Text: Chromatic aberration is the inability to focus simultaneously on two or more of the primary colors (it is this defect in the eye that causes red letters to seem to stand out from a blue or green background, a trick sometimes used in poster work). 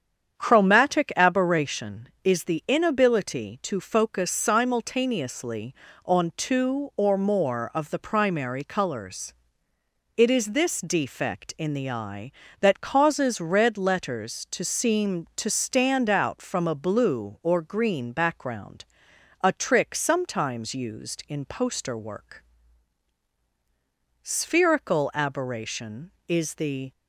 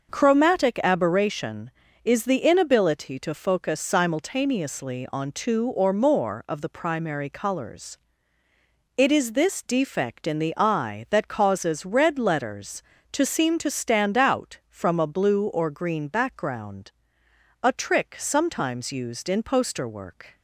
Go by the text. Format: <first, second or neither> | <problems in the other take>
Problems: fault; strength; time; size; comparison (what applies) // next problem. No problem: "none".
second | starts louder than the rest; strong; until 1.4 s; 8 dB // goes on to say "Spherical aberration is the"; strong; from 24.2 s on; 2.7 s long